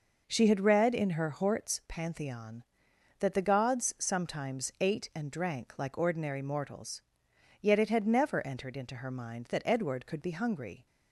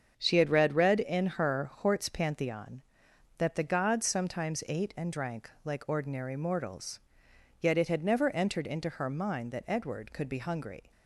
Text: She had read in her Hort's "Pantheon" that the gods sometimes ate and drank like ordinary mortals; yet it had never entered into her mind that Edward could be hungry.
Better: first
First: none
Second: starts louder than the rest; until 1.1 s; 7 dB // says "read" twice; at 0.7 s // pauses between "drank" and "like"; slight; at 5.4 s; 0.16 s long

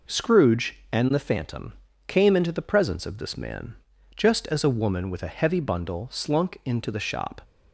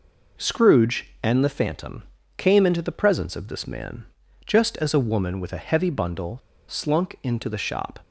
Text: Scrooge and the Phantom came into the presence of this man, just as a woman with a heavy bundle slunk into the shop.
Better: first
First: pauses between "Phantom" and "came"; slight; at 1.7 s; 0.34 s long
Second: pauses between "Phantom" and "came"; slight; at 2.0 s; 0.34 s long // pauses between "bundle" and "slunk"; slight; at 6.3 s; 0.32 s long

